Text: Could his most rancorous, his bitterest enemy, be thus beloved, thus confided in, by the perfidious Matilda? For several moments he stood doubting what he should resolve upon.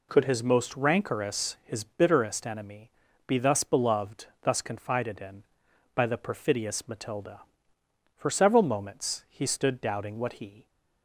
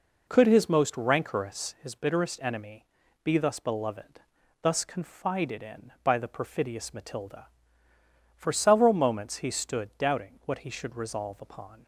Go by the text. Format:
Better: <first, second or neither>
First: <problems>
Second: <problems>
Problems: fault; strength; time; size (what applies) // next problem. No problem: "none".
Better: second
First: stops before "should resolve upon"; at 10.6 s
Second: none